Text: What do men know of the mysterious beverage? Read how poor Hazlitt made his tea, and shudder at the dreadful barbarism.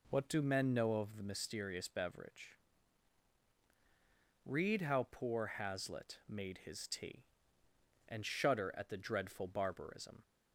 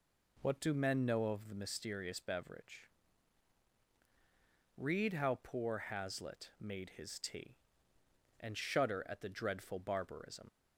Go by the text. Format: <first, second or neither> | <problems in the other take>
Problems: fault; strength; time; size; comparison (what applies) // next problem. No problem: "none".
first | leaves "barbarism" unfinished; at 10.4 s; 40 ms